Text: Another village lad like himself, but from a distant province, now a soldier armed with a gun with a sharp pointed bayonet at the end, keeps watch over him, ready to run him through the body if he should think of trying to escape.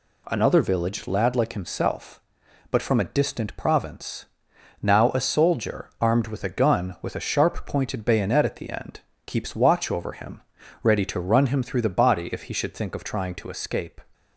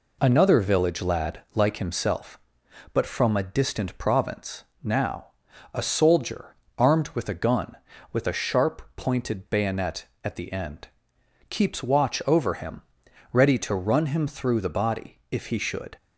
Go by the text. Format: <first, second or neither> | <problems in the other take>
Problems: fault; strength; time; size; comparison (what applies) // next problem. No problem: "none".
first | pauses between "now" and "a"; noticeable; at 5.2 s; 0.46 s long // pauses between "soldier" and "armed"; slight; at 6.5 s; 0.22 s long // pauses between "sharp" and "pointed"; slight; at 8.8 s; 0.16 s long // stops before "think of trying to escape"; at 15.9 s